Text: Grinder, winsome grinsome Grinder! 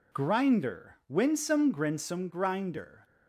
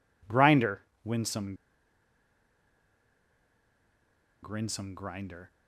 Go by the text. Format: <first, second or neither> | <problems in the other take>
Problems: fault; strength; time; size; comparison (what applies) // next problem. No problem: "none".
first | pauses between "winsome" and "grinsome"; strong; at 1.5 s; 2.8 s long